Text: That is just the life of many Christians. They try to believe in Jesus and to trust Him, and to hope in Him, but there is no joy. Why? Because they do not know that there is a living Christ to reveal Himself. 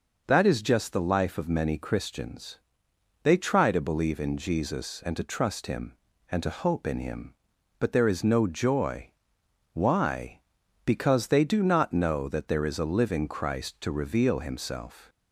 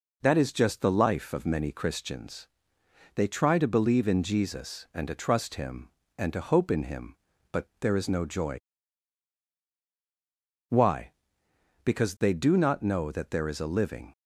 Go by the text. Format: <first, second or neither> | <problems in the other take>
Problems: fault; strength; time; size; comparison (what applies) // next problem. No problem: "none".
first | stops before "Christ to reveal Himself"; at 14.1 s